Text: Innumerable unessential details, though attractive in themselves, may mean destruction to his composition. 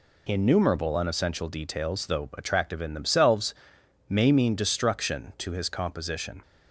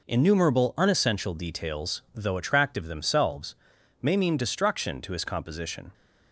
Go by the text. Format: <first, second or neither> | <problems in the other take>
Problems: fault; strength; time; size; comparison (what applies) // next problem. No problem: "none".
first | skips "in"; at 2.8 s